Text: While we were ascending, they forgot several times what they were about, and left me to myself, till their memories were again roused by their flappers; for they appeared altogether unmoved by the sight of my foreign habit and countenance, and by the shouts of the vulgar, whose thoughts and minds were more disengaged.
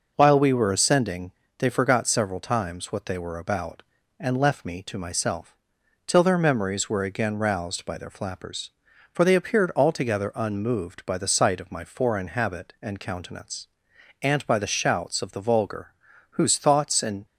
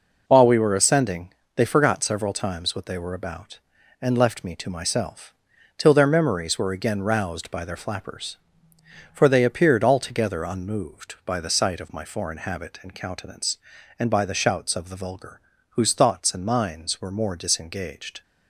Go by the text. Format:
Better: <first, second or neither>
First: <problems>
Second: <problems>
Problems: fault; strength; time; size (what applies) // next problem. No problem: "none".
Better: second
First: stops before "minds were more disengaged"; at 17.2 s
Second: none